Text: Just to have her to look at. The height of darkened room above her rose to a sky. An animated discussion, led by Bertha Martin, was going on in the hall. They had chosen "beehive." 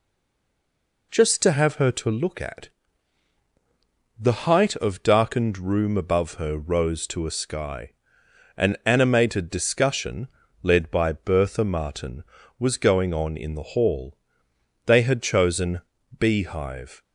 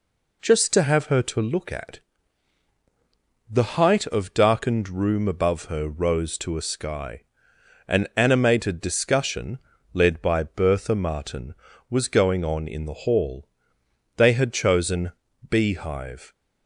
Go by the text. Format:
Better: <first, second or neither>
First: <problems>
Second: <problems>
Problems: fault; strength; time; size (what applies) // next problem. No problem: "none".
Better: second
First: stays silent before the first word; until 1.1 s; 1.1 s long // pauses between "chosen" and "beehive"; at 15.8 s; 0.38 s long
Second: pauses between "chosen" and "beehive"; at 15.1 s; 0.38 s long